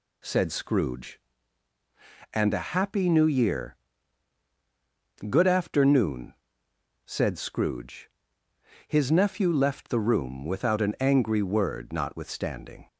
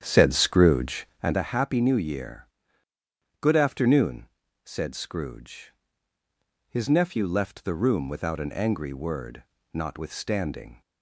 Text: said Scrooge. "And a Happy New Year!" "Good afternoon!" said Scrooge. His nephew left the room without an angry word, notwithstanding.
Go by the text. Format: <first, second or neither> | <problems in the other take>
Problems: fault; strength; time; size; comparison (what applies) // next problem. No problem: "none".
first | starts louder than the rest; strong; until 1.4 s; 9 dB